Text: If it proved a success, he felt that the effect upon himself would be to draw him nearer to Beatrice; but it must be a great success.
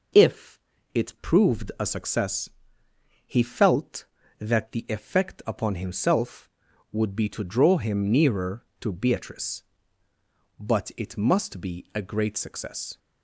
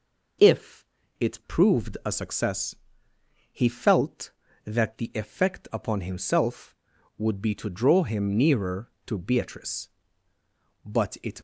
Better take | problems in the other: first | pauses between "If" and "it"; slight; at 0.8 s; 0.32 s long; slight in the first // stops before "must be a great success"; at 11.3 s

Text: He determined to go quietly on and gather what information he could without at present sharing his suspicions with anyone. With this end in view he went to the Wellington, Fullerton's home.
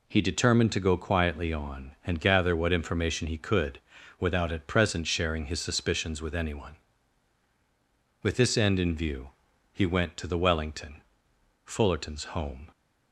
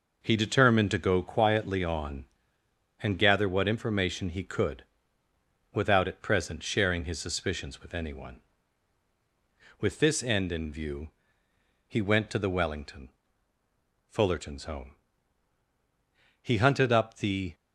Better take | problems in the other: first | pauses between "could" and "without"; noticeable; at 4.8 s; 0.90 s long; also in the first // pauses between "view" and "he"; noticeable; at 11.0 s; 0.80 s long; also in the first // goes on to say "He hunted up the"; noticeable; from 16.4 s on; 1.1 s long

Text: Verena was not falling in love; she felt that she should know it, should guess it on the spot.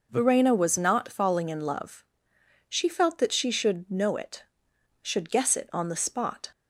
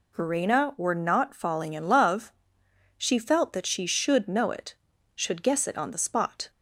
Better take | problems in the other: first | says "were" for "was"; at 0.7 s

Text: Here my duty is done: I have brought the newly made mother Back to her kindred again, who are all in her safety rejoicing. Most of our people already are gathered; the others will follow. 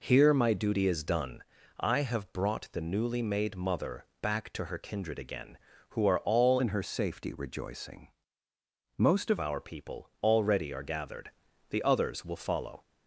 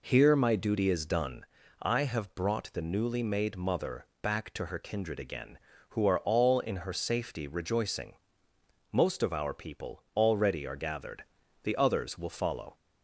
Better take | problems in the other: second | pauses between "mother" and "Back"; slight; at 4.0 s; 0.16 s long; slight in the second // changes voice from "in" to "of"; from 6.5 to 9.3 s; 2.8 s long

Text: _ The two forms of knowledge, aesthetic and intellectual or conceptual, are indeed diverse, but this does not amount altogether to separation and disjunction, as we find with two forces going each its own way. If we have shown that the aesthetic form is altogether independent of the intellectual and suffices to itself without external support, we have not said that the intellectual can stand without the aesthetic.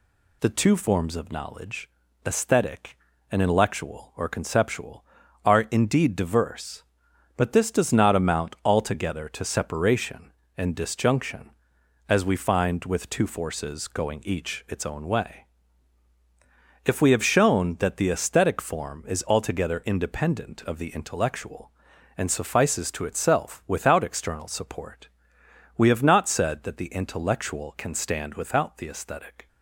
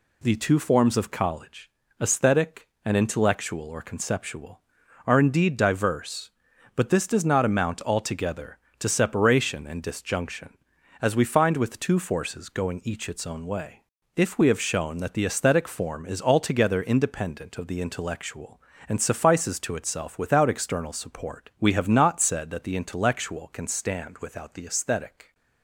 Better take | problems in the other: first | says "college" for "knowledge"; at 1.1 s

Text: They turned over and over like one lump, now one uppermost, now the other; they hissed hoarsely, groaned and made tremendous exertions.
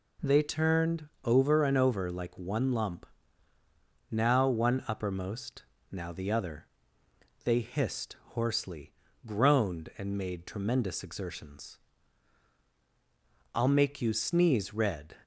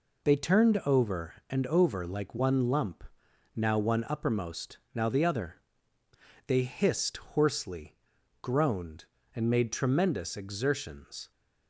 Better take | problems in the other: second | pauses between "turned" and "over"; slight; at 1.0 s; 0.16 s long // pauses between "hissed" and "hoarsely"; slight; at 8.1 s; 0.16 s long // goes on to say "I'll make you sneeze red"; from 13.5 s on; 1.6 s long

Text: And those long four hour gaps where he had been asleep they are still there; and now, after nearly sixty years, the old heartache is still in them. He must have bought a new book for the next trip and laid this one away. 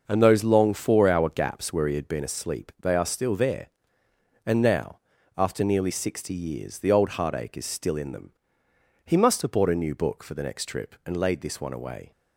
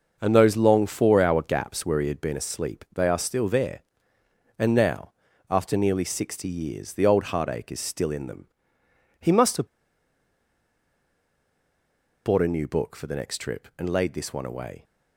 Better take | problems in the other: first | pauses between "have" and "bought"; strong; at 9.6 s; 2.5 s long

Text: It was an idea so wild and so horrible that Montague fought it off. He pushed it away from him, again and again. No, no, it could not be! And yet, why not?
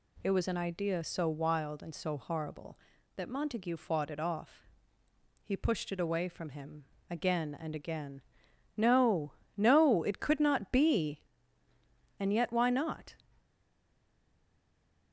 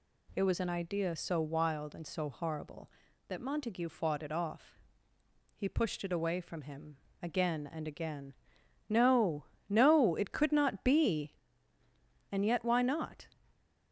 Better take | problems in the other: second | stays silent after the last word; noticeable; from 13.3 s on; 1.8 s long

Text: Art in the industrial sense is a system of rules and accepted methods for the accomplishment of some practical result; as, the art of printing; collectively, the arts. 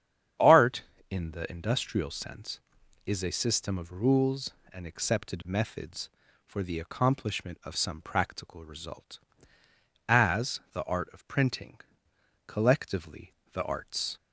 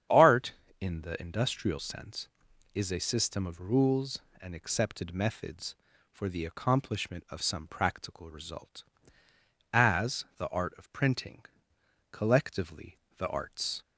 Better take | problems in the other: neither | starts louder than the rest; strong; the same in both

